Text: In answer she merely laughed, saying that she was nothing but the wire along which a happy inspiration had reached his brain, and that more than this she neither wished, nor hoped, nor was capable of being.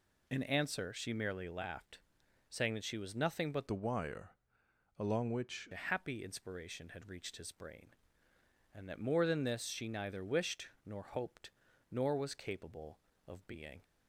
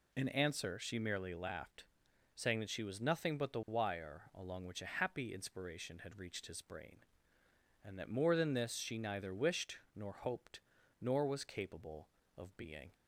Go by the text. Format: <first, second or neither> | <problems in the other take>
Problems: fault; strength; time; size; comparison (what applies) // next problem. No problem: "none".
second | changes voice from "the" to "which"; from 3.6 to 5.6 s; 2.0 s long // pauses between "wire" and "along"; noticeable; at 4.3 s; 0.64 s long